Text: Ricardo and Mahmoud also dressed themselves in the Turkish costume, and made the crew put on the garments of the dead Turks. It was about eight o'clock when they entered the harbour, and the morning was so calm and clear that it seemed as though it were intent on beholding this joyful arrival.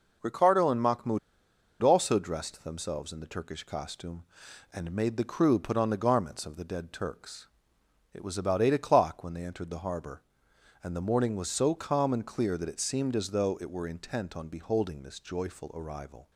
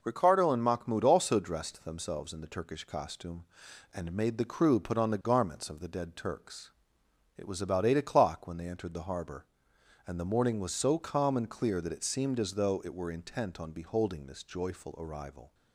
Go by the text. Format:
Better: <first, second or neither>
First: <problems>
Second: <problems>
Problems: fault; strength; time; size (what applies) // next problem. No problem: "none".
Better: second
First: pauses between "Mahmoud" and "also"; noticeable; at 1.1 s; 0.63 s long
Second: none